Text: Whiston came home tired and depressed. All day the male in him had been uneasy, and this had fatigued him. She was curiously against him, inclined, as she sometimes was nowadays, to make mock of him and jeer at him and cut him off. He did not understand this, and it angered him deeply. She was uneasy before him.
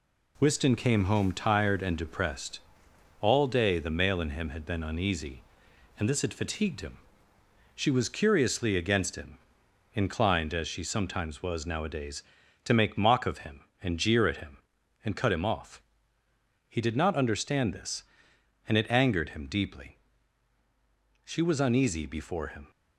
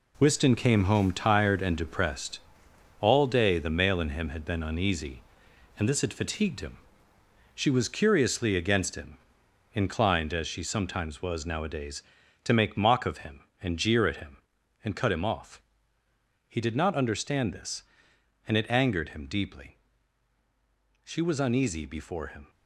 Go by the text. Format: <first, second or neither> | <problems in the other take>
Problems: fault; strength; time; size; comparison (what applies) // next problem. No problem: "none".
first | gets quieter; strong; throughout; 7.5 dB